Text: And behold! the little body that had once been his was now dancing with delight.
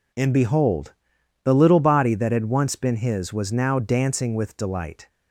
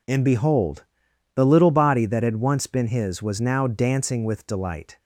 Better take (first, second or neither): neither